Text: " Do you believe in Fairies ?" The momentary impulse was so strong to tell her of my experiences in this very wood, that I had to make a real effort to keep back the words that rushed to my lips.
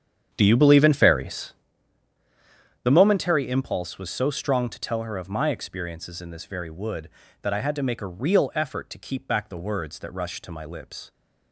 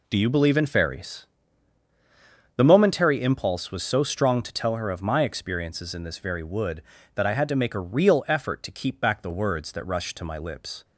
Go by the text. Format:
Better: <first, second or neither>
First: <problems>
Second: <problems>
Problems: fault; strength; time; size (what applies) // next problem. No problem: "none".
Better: second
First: starts louder than the rest; strong; until 1.7 s; 8 dB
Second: none